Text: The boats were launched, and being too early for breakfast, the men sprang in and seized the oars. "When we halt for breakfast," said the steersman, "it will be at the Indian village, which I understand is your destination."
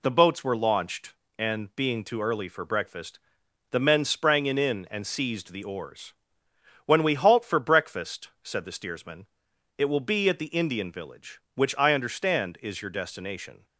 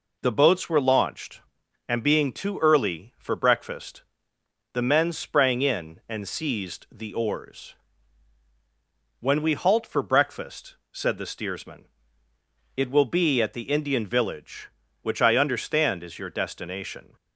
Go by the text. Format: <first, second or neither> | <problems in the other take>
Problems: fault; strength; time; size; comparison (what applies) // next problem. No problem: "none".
second | says "in" twice; at 4.5 s